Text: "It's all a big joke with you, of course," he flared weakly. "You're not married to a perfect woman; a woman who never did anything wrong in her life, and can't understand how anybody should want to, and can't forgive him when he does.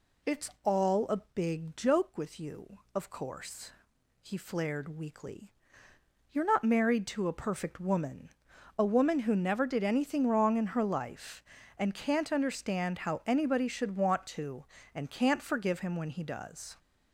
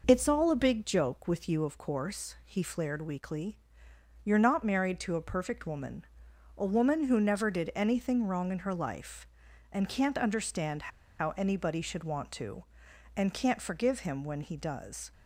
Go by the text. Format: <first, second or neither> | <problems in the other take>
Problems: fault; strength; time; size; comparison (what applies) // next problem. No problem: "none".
first | pauses between "understand" and "how"; slight; at 10.9 s; 0.31 s long